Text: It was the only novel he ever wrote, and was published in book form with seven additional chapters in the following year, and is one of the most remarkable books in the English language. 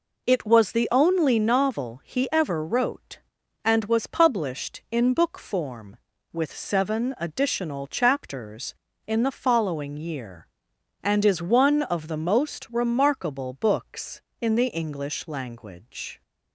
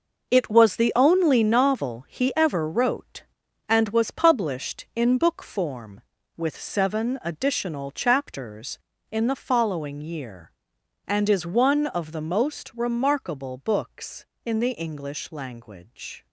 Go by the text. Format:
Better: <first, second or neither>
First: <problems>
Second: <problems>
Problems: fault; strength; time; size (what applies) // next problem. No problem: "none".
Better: first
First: none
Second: gets quieter; strong; throughout; 10.5 dB